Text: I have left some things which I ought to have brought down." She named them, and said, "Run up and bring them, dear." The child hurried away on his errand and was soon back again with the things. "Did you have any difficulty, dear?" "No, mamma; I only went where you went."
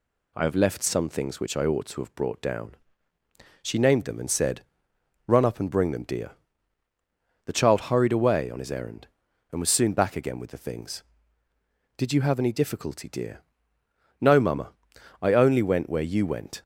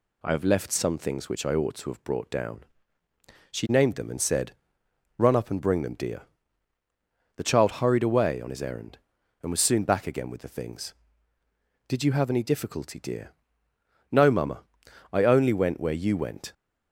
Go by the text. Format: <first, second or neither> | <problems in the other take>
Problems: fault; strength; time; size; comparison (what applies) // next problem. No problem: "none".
neither | none